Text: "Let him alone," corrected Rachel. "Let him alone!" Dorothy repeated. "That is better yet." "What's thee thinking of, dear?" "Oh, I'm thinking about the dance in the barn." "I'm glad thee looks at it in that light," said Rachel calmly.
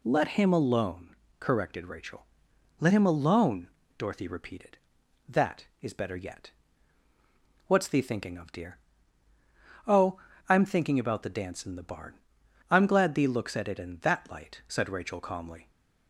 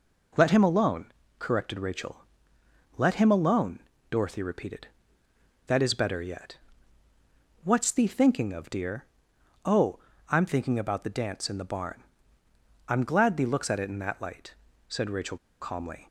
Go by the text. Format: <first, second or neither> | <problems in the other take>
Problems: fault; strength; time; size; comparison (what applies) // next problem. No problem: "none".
first | pauses between "Rachel" and "calmly"; slight; at 15.3 s; 0.24 s long